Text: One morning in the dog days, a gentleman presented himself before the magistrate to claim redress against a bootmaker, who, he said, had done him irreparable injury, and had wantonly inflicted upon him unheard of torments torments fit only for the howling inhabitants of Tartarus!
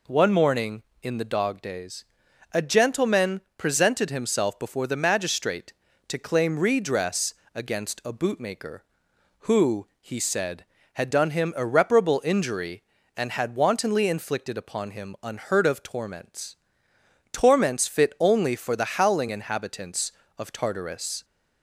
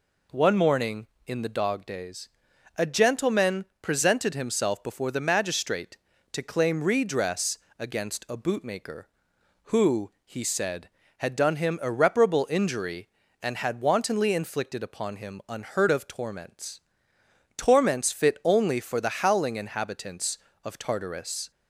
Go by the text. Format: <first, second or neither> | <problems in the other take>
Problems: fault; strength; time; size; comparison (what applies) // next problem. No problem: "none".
neither | pauses between "gentleman" and "presented"; slight; the same in both // pauses between "redress" and "against"; slight; the same in both // pauses between "torments" and "torments"; noticeable; the same in both